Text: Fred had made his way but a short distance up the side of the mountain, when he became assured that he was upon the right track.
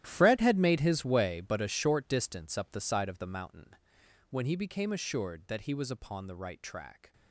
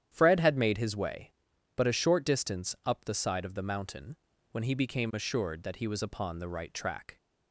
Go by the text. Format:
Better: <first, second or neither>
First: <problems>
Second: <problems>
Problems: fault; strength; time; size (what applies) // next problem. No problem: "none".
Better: second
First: gets quieter; strong; throughout; 15.5 dB // starts louder than the rest; strong; until 1.0 s; 13 dB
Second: starts louder than the rest; strong; until 1.1 s; 10 dB